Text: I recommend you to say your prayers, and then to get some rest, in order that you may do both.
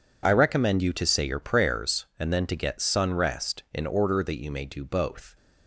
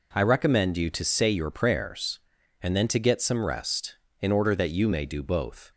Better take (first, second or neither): second